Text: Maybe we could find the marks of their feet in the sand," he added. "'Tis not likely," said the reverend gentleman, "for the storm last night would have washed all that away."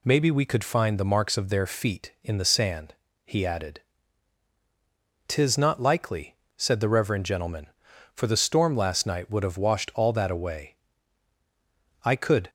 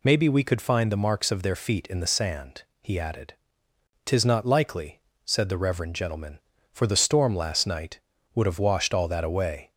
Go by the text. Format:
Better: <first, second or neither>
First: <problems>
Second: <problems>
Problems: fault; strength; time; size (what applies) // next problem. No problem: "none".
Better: second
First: goes on to say "I could"; slight; from 12.0 s on; 0.46 s long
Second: none